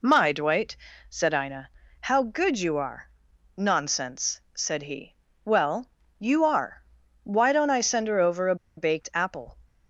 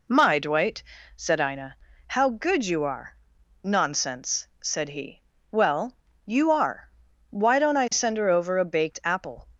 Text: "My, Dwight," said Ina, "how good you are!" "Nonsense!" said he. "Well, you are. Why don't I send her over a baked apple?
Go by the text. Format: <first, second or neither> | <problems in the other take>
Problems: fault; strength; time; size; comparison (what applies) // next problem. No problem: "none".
second | pauses between "a" and "baked"; slight; at 8.5 s; 0.21 s long